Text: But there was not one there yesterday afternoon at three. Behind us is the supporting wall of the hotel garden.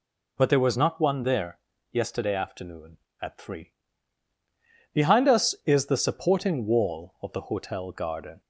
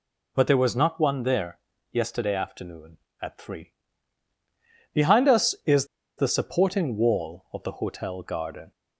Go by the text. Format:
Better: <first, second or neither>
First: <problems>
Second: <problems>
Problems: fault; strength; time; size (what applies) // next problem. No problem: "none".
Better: first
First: pauses between "there" and "yesterday"; slight; at 1.5 s; 0.32 s long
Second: pauses between "there" and "yesterday"; slight; at 1.5 s; 0.32 s long // pauses between "is" and "the"; slight; at 5.8 s; 0.31 s long